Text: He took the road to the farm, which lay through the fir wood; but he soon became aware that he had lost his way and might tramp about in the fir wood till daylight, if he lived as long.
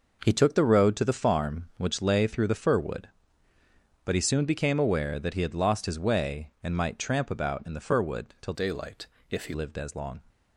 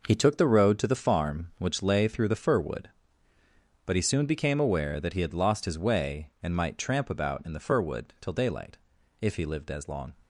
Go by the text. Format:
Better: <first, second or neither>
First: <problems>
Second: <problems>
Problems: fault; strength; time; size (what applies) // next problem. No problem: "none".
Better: second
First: changes voice from "daylight" to "he"; from 8.5 to 9.5 s; 1.0 s long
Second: none